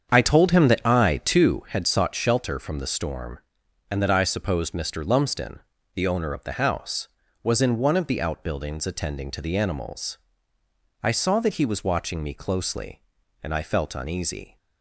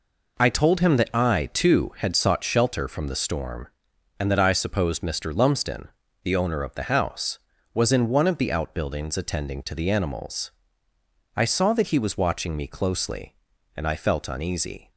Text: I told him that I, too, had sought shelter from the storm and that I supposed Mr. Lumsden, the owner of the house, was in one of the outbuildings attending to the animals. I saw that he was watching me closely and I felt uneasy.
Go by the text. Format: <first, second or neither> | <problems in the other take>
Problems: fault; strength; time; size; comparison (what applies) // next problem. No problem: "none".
second | starts louder than the rest; strong; until 1.6 s; 7.5 dB